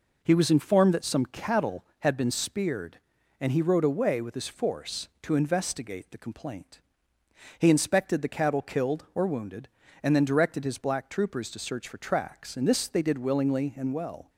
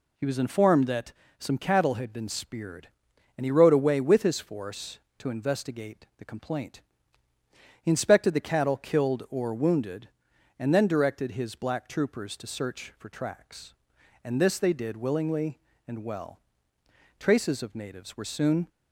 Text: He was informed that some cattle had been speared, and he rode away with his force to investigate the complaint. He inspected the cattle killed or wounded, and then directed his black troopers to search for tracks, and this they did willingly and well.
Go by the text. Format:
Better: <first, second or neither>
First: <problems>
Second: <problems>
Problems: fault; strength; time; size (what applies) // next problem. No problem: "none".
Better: first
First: none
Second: pauses between "that" and "some"; slight; at 1.1 s; 0.26 s long // goes on to say "Traces of natives were soon"; from 17.1 s on; 1.5 s long